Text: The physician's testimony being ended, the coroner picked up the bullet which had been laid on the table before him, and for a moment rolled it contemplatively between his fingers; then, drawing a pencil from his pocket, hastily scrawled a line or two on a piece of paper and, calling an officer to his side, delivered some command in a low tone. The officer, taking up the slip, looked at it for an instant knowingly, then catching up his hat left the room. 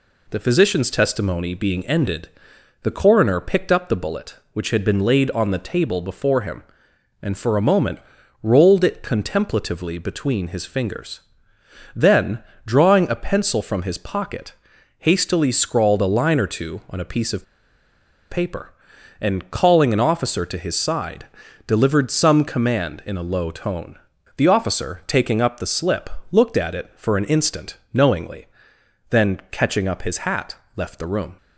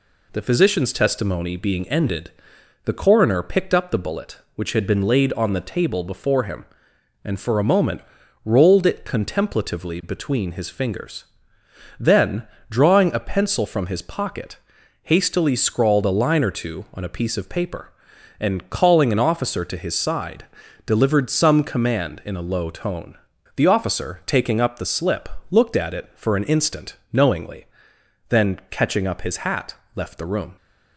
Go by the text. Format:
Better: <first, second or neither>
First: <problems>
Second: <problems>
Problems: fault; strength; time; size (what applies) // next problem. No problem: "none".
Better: second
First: pauses between "moment" and "rolled"; at 7.9 s; 0.42 s long // pauses between "of" and "paper"; noticeable; at 17.4 s; 0.85 s long // pauses between "instant" and "knowingly"; slight; at 27.7 s; 0.16 s long // pauses between "hat" and "left"; slight; at 30.5 s; 0.20 s long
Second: pauses between "moment" and "rolled"; at 8.0 s; 0.42 s long // pauses between "instant" and "knowingly"; slight; at 26.9 s; 0.16 s long // pauses between "hat" and "left"; slight; at 29.7 s; 0.20 s long